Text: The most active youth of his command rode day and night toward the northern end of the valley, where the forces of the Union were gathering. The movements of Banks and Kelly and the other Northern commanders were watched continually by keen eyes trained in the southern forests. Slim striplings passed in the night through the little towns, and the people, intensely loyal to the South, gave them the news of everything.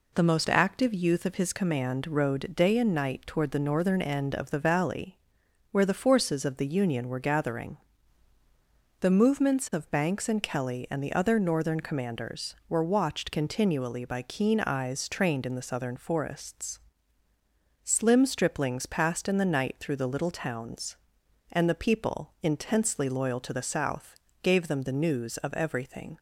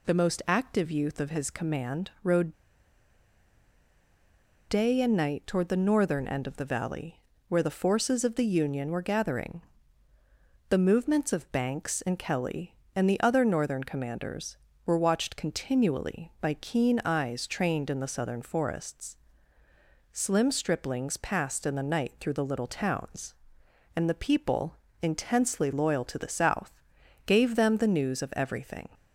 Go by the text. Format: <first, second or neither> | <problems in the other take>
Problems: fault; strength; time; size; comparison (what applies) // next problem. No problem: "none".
first | pauses between "rode" and "day"; strong; at 2.5 s; 2.1 s long